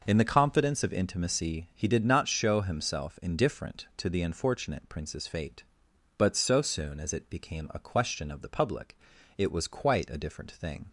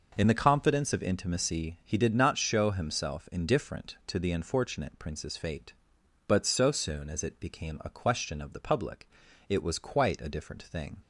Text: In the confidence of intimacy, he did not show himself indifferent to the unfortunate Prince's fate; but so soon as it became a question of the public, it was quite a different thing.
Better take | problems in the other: neither | none

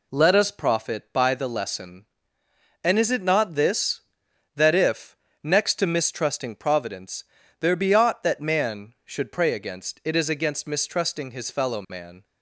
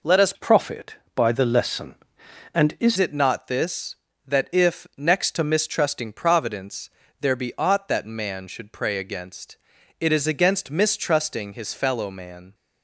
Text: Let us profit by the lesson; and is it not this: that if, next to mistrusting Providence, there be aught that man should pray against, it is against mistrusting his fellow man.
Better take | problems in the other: first | changes voice from "profit" to "is"; from 0.3 to 2.9 s; 2.6 s long

